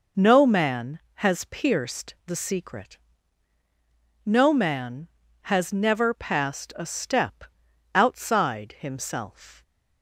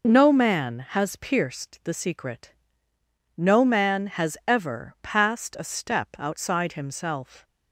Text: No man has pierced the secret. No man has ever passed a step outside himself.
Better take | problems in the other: second | says "never" for "ever"; at 5.7 s // pauses between "step" and "outside"; noticeable; at 7.4 s; 0.50 s long

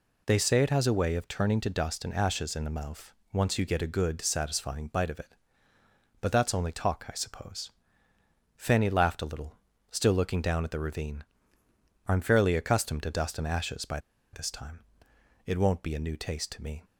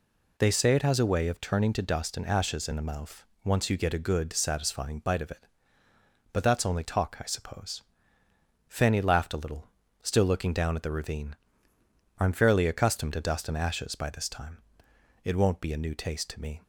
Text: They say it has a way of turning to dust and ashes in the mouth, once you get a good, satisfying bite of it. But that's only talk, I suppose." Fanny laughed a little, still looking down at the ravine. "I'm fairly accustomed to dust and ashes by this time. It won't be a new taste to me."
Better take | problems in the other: second | pauses between "by" and "this"; slight; at 13.9 s; 0.34 s long

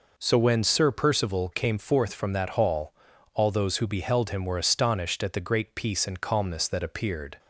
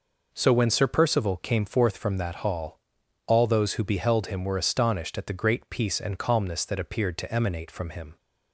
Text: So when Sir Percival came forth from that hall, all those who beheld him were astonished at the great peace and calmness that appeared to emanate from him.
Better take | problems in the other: second | stops before "to emanate from him"; at 7.3 s

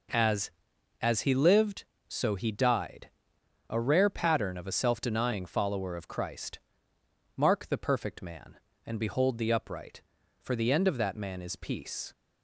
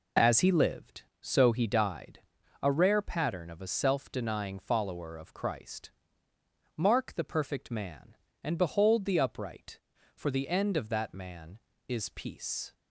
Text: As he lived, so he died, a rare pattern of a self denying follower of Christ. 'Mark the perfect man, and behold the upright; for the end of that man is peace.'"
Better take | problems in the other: second | says "As" twice; at 0.9 s

